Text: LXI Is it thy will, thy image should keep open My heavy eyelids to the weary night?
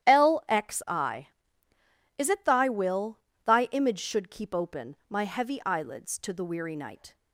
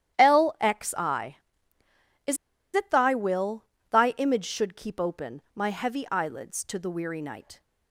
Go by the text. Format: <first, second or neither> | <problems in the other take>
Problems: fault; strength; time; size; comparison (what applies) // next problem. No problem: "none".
first | starts louder than the rest; strong; until 1.2 s; 11.5 dB; strong in the first // pauses between "Is" and "it"; at 2.3 s; 0.38 s long